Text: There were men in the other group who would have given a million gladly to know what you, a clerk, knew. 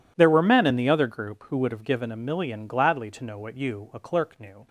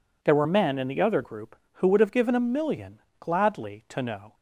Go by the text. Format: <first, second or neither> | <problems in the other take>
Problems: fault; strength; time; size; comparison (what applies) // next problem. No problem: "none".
first | pauses between "million" and "gladly"; slight; at 2.9 s; 0.20 s long // stops before "what you a clerk knew"; at 4.3 s